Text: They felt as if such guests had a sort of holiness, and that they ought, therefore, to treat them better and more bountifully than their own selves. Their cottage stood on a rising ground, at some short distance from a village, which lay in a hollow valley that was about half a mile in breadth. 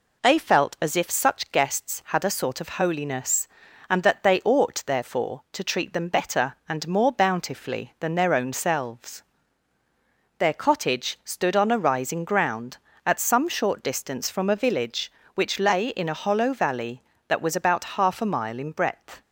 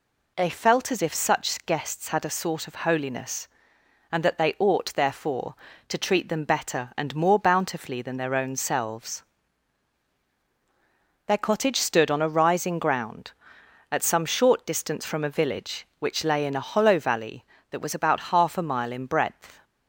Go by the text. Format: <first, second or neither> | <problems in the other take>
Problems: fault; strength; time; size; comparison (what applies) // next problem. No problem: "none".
neither | none